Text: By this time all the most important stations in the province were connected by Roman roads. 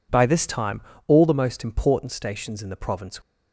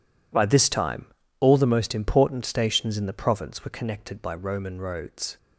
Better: second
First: pauses between "time" and "all"; slight; at 0.8 s; 0.24 s long // stops before "were connected by Roman roads"; at 3.2 s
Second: pauses between "time" and "all"; slight; at 1.0 s; 0.34 s long

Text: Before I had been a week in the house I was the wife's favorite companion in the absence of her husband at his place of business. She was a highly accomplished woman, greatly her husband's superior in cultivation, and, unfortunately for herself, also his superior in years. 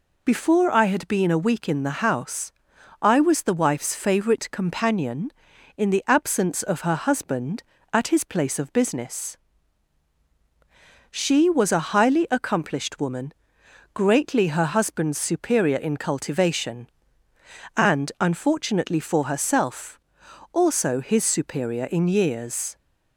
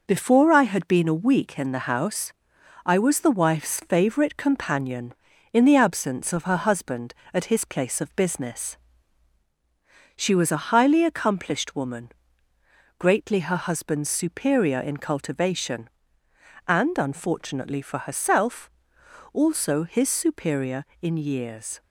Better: first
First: pauses between "house" and "I"; noticeable; at 2.5 s; 0.48 s long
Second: gets quieter; noticeable; throughout; 4.5 dB // pauses between "house" and "I"; noticeable; at 2.3 s; 0.52 s long

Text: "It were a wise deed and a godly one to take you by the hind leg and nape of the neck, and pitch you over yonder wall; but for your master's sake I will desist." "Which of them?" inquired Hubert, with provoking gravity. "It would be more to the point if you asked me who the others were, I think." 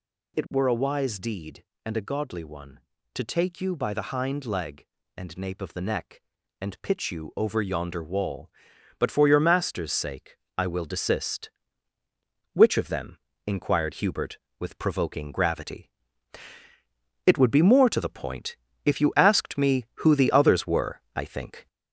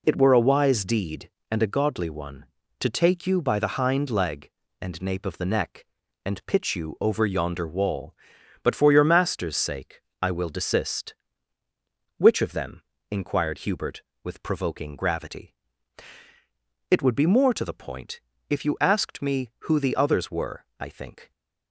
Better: second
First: gets louder; noticeable; throughout; 4 dB // pauses between "sake" and "I"; slight; at 10.3 s; 0.20 s long // pauses between "point" and "if"; slight; at 18.5 s; 0.30 s long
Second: pauses between "sake" and "I"; slight; at 10.0 s; 0.20 s long // pauses between "point" and "if"; slight; at 18.1 s; 0.30 s long

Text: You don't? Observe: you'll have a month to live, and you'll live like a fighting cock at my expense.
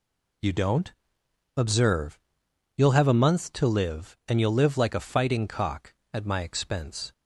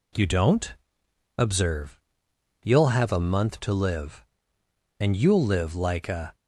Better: first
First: none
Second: stops before "fighting cock at my expense"; at 6.3 s

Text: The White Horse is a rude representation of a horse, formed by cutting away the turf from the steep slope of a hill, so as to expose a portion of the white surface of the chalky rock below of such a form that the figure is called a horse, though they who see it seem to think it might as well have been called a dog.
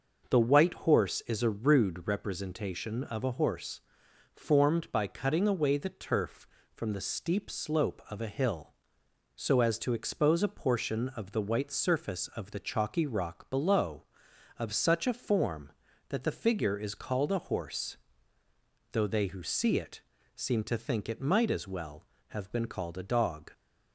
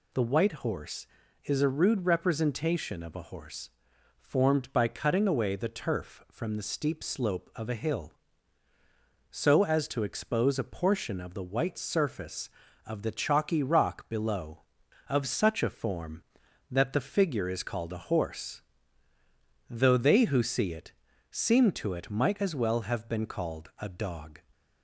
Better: first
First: pauses between "it" and "seem"; slight; at 20.0 s; 0.34 s long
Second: pauses between "it" and "seem"; at 20.9 s; 0.40 s long // skips "think"; at 21.9 s

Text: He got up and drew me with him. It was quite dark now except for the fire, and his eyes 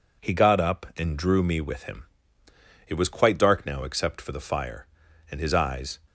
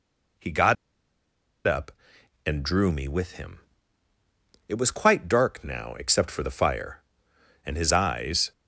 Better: first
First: none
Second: pauses between "got" and "up"; noticeable; at 0.7 s; 0.92 s long

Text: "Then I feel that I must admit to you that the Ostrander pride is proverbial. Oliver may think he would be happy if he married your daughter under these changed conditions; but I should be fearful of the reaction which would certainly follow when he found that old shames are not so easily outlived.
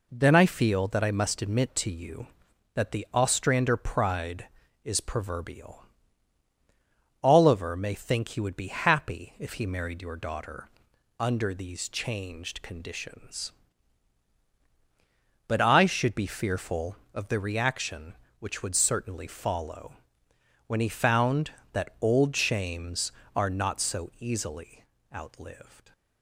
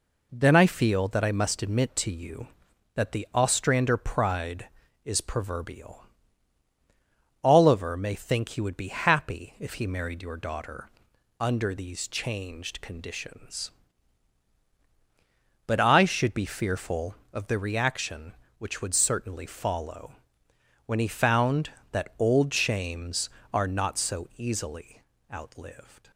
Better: neither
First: pauses between "daughter" and "under"; noticeable; at 10.6 s; 0.50 s long // pauses between "follow" and "when"; noticeable; at 19.9 s; 0.70 s long // pauses between "easily" and "outlived"; slight; at 24.8 s; 0.31 s long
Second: pauses between "daughter" and "under"; noticeable; at 10.8 s; 0.50 s long // pauses between "follow" and "when"; noticeable; at 20.1 s; 0.70 s long // pauses between "easily" and "outlived"; slight; at 25.0 s; 0.32 s long

